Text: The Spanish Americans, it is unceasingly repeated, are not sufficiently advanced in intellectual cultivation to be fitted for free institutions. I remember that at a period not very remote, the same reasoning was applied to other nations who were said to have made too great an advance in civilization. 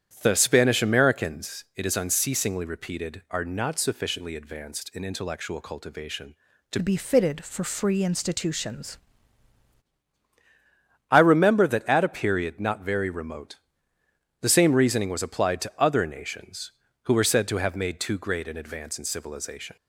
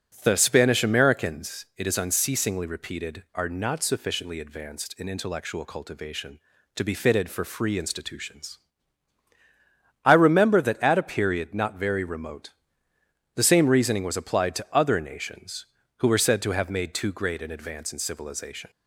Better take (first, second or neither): second